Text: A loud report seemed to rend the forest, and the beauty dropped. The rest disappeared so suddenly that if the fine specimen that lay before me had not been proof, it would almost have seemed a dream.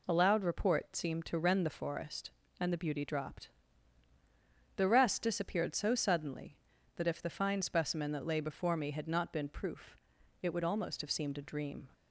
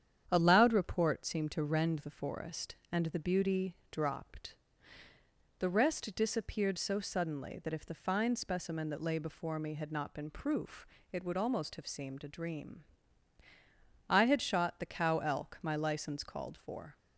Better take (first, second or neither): first